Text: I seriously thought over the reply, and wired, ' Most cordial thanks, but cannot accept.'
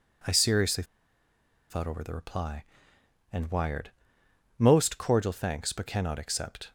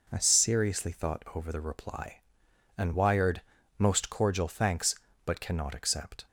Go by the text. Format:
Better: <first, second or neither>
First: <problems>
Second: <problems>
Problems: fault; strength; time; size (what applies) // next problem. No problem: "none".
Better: second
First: pauses between "seriously" and "thought"; noticeable; at 0.8 s; 0.85 s long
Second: none